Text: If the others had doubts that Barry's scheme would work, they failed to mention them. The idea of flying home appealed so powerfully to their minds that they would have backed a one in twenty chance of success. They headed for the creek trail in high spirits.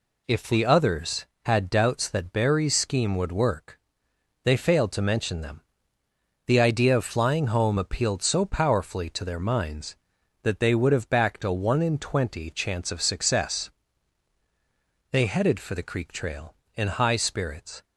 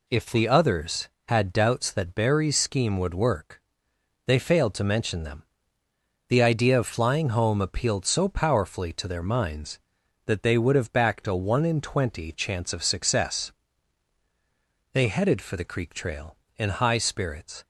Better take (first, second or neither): neither